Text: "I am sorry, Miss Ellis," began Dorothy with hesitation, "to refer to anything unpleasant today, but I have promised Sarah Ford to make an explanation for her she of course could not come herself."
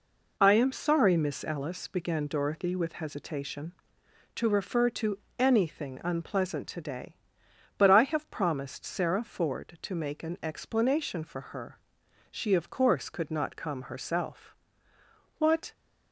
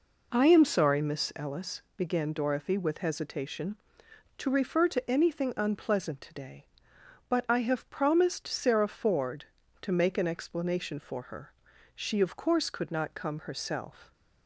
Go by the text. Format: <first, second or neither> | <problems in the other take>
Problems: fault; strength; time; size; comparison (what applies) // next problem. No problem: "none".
second | pauses between "to" and "anything"; slight; at 5.1 s; 0.22 s long // pauses between "her" and "she"; noticeable; at 11.7 s; 0.52 s long; also in the second // goes on to say "What"; slight; from 15.3 s on; 0.34 s long